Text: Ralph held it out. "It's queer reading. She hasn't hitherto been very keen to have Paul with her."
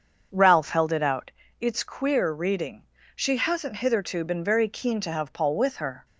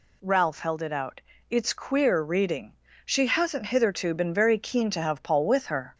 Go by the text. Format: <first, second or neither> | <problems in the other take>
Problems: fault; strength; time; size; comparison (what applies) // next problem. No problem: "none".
second | starts louder than the rest; until 1.4 s; 6.5 dB